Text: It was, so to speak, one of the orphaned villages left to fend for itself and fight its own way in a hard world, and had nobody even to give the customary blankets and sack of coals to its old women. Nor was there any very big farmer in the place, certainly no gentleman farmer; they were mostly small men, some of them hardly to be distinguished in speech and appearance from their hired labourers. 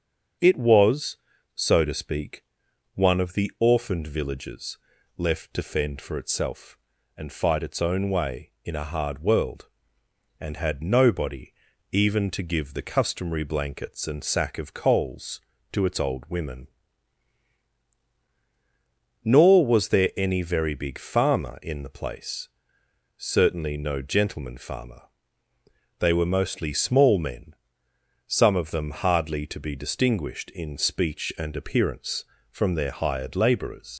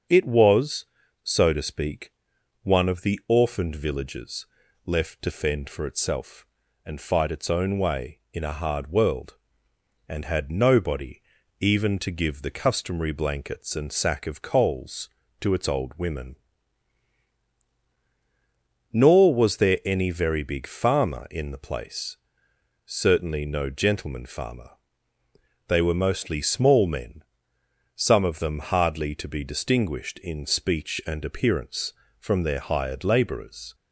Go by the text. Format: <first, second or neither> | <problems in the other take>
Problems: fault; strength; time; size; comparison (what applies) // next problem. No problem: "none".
second | starts louder than the rest; strong; until 1.7 s; 7 dB; strong in the second // pauses between "villages" and "left"; at 4.7 s; 0.38 s long; also in the second // pauses between "nobody" and "even"; at 11.5 s; 0.40 s long; also in the second // leaves "labourers" unfinished; at 33.9 s; 80 ms